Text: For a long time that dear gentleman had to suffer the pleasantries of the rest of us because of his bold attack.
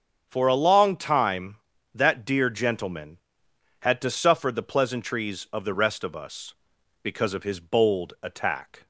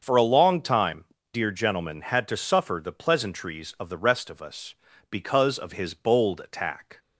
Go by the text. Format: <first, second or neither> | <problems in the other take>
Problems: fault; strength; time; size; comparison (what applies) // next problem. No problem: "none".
first | starts louder than the rest; until 1.0 s; 6.5 dB; strong in the first // skips "that"; at 1.1 s